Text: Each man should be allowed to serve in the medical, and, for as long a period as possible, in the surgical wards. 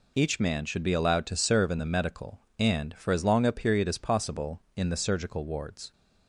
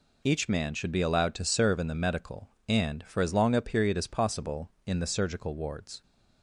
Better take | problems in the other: neither | none

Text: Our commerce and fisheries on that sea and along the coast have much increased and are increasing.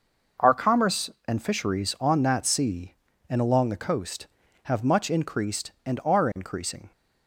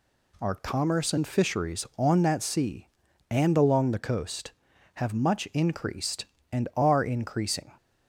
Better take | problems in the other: neither | none

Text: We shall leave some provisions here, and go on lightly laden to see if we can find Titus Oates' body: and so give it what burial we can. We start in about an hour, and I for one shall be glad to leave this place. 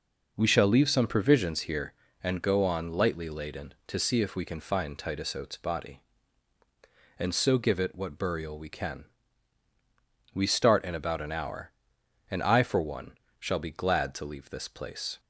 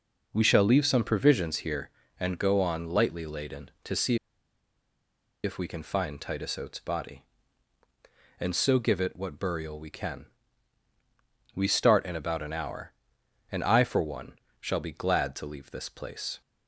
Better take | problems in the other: first | pauses between "see" and "if"; strong; at 4.1 s; 1.2 s long // pauses between "one" and "shall"; slight; at 14.3 s; 0.28 s long; slight in the first

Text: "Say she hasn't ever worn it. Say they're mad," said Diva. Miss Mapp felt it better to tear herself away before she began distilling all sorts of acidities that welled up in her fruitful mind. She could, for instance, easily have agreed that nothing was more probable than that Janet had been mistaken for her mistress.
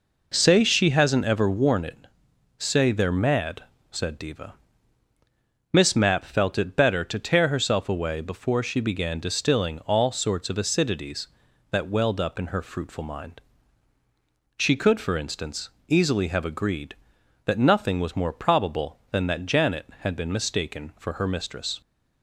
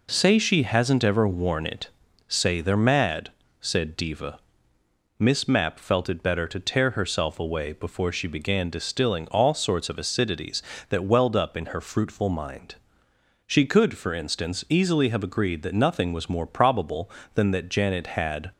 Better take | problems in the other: first | stops before "been mistaken for her mistress"; at 18.5 s

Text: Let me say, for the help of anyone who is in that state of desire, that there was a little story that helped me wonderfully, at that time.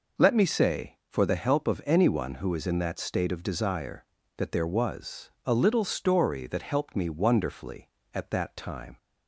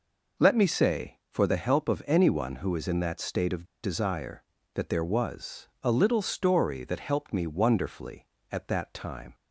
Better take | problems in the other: first | pauses between "of" and "desire"; slight; at 3.6 s; 0.20 s long // pauses between "was" and "a"; slight; at 5.6 s; 0.16 s long; slight in the first

